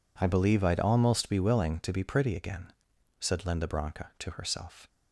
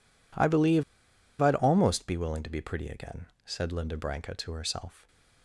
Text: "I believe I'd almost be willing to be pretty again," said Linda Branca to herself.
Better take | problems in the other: first | pauses between "believe" and "I'd"; noticeable; at 0.8 s; 0.55 s long

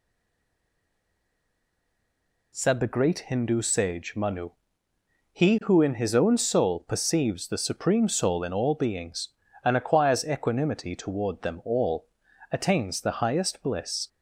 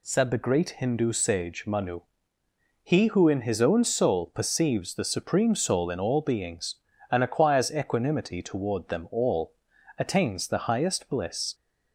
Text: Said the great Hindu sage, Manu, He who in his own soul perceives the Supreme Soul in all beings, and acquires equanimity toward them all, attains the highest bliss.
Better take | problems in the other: second | stays silent before the first word; until 2.5 s; 2.5 s long

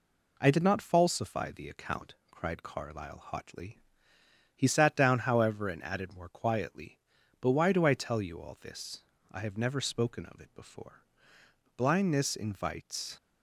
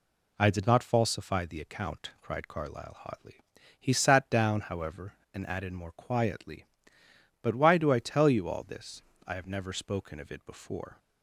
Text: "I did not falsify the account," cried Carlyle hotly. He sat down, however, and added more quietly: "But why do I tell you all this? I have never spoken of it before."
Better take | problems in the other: second | goes on to say "Blindness invites"; from 11.7 s on; 1.3 s long

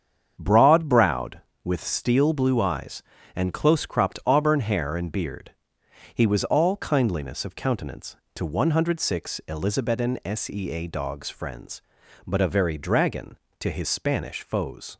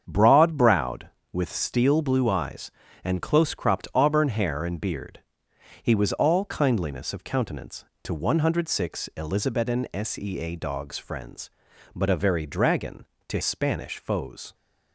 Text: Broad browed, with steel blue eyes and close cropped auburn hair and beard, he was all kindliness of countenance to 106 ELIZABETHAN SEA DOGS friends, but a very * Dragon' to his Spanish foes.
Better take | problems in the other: first | starts louder than the rest; strong; until 1.0 s; 7.5 dB; strong in the first // skips "his"; at 13.4 s

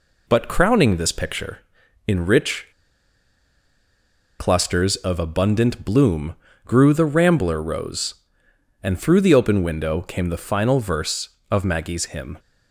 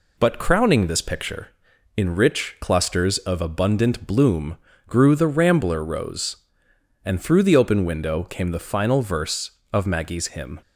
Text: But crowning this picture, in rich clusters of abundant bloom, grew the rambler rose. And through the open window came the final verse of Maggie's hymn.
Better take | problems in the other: second | pauses between "rich" and "clusters"; strong; at 2.6 s; 1.7 s long

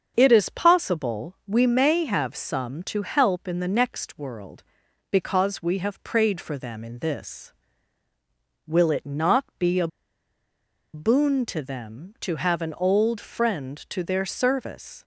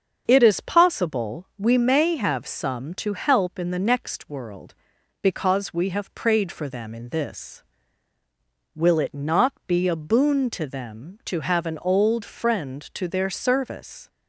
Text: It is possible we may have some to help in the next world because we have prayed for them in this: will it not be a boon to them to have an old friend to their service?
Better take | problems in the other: second | starts louder than the rest; until 1.1 s; 7 dB; also in the second // pauses between "not" and "be"; slight; at 9.4 s; 0.16 s long; slight in the second // pauses between "a" and "boon"; at 9.8 s; 1.0 s long

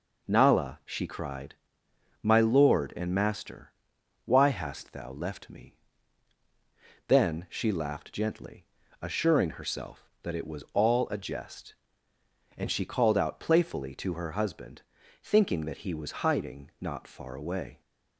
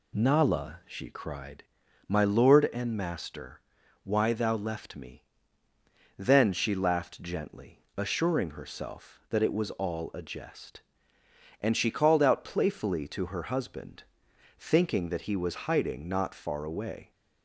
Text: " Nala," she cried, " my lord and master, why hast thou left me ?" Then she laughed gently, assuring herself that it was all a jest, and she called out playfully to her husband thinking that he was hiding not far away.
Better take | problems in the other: first | skips "hast"; at 4.3 s // pauses between "husband" and "thinking"; noticeable; at 14.0 s; 0.52 s long; also in the first

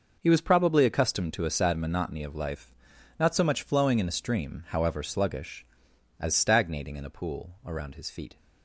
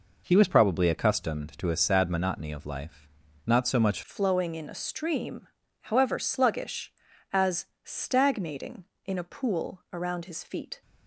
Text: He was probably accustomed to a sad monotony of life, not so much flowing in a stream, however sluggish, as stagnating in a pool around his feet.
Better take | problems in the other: first | changes voice at "flowing"; from 4.0 s on; 6.8 s long // pauses between "as" and "stagnating"; slight; at 7.6 s; 0.16 s long

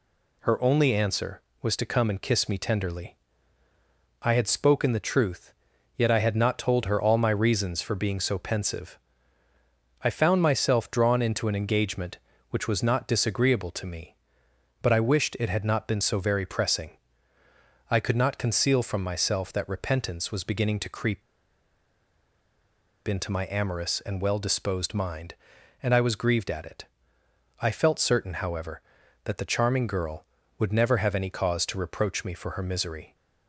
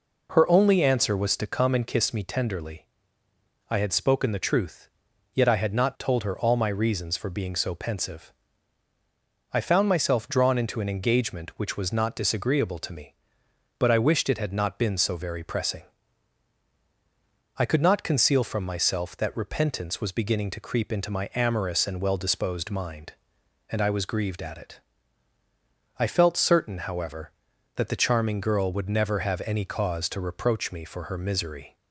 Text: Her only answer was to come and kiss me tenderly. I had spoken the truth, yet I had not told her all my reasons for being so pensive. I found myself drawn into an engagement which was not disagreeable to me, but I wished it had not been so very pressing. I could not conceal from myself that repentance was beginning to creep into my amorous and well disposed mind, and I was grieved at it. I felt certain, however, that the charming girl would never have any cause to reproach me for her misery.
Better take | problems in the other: second | pauses between "creep" and "into"; strong; at 21.2 s; 1.8 s long

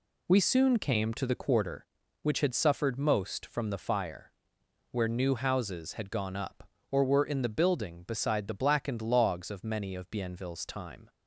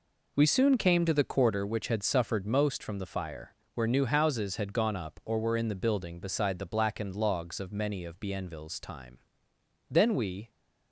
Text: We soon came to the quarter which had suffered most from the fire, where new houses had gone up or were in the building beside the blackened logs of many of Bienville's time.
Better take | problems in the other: first | goes on to say "Then we"; from 9.8 s on; 0.60 s long

